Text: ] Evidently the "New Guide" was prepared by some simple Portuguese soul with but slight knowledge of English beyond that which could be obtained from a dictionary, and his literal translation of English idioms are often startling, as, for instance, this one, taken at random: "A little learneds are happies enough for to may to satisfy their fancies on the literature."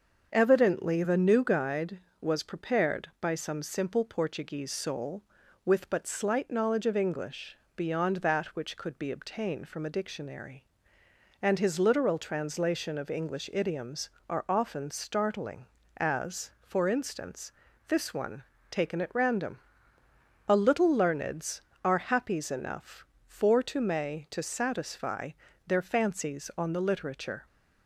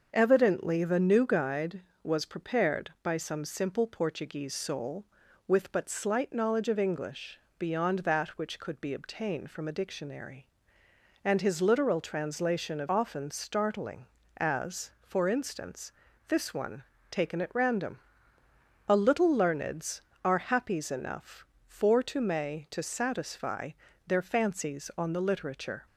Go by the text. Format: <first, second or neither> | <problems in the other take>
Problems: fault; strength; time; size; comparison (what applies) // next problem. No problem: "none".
first | starts louder than the rest; until 1.1 s; 6.5 dB; also in the first // pauses between "English" and "beyond"; slight; at 7.3 s; 0.20 s long; slight in the first // skips "English idioms are"; at 12.8 s // pauses between "satisfy" and "their"; slight; at 23.7 s; 0.34 s long; slight in the first